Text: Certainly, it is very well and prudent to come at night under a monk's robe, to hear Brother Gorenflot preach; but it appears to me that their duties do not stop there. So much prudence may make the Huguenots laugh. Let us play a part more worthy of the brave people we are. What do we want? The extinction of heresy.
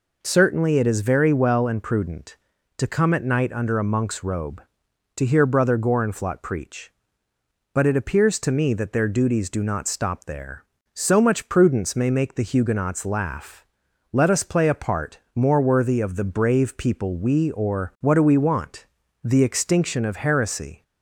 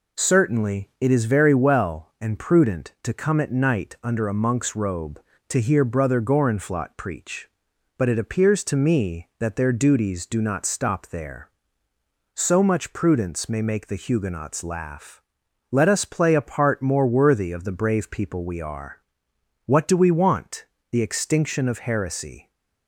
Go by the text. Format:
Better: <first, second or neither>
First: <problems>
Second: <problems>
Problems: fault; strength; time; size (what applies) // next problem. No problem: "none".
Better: second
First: pauses between "part" and "more"; slight; at 15.1 s; 0.18 s long // says "or" for "are"; at 17.5 s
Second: none